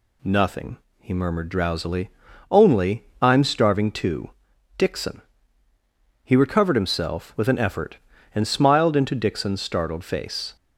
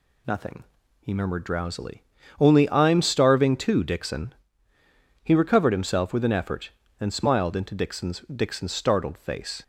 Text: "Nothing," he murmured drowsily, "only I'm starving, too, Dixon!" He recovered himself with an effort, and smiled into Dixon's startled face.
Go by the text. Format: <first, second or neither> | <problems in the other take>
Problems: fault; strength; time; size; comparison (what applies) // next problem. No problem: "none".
first | says "Dixon's" twice; at 8.2 s